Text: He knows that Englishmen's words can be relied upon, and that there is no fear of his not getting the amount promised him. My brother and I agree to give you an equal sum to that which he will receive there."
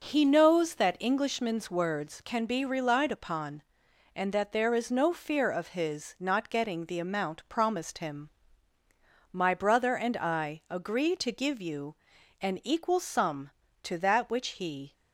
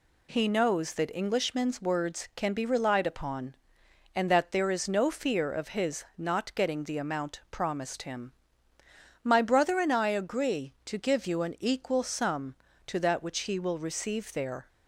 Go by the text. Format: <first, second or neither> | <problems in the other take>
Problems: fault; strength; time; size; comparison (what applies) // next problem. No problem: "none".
second | pauses between "you" and "an"; noticeable; at 11.9 s; 0.46 s long // stops before "will receive there"; at 14.9 s